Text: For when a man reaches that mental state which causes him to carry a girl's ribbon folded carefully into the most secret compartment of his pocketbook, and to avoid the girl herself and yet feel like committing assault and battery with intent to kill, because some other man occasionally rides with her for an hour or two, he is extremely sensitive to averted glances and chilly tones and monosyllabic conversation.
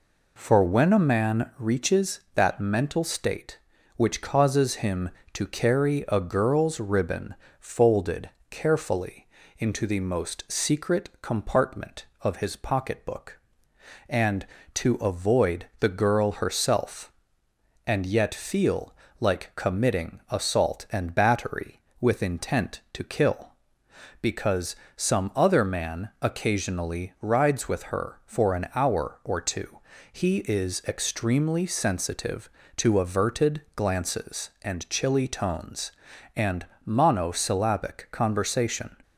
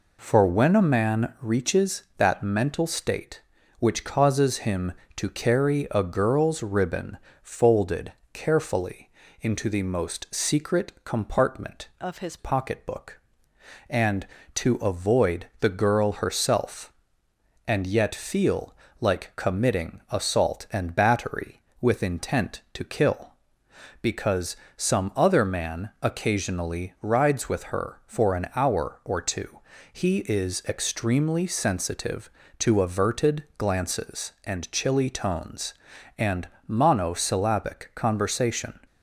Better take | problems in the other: first | pauses between "ribbon" and "folded"; slight; at 7.1 s; 0.26 s long; slight in the first // pauses between "folded" and "carefully"; slight; at 8.1 s; 0.22 s long; slight in the first // pauses between "carefully" and "into"; slight; at 9.0 s; 0.30 s long; slight in the first // changes voice from "of" to "his"; from 12.0 to 12.3 s; 0.3 s long // pauses between "feel" and "like"; slight; at 18.7 s; 0.26 s long; slight in the first // pauses between "because" and "some"; slight; at 24.5 s; 0.20 s long; slight in the first // pauses between "averted" and "glances"; slight; at 33.4 s; 0.16 s long; slight in the first // pauses between "and" and "monosyllabic"; slight; at 36.4 s; 0.20 s long; slight in the first

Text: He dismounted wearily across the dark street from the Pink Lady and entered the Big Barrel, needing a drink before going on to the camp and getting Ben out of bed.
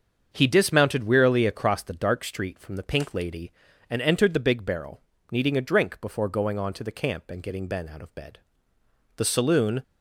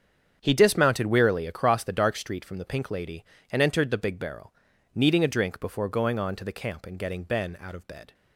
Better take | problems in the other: second | starts louder than the rest; until 1.3 s; 7 dB; strong in the second // goes on to say "The saloon"; noticeable; from 9.1 s on; 0.66 s long

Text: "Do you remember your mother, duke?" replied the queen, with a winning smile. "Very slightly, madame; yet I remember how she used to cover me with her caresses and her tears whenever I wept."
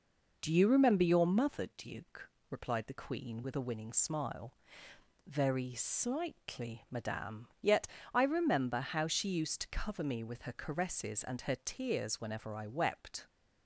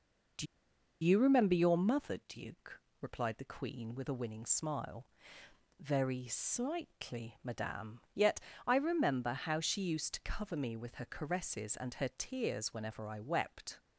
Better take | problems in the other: first | pauses between "Do" and "you"; noticeable; at 0.4 s; 0.58 s long // pauses between "yet" and "I"; slight; at 8.3 s; 0.26 s long; slight in the first

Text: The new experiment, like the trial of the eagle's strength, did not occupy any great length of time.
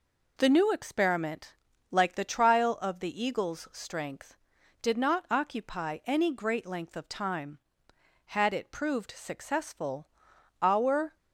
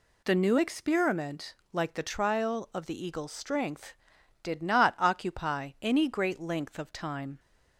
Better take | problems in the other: second | goes on to say "Had it proved successful our"; strong; from 8.2 s on; 2.9 s long

